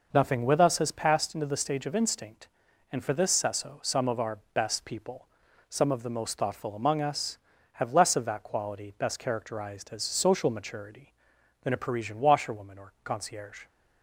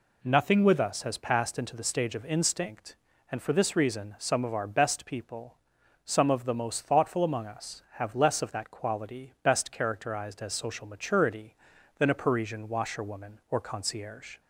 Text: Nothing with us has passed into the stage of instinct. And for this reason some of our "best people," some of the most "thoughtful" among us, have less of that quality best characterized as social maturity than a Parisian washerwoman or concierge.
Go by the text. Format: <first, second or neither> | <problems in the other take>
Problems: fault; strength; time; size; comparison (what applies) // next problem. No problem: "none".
second | says "sesso" for "reason"; at 3.3 s // pauses between "our" and "best"; slight; at 4.3 s; 0.16 s long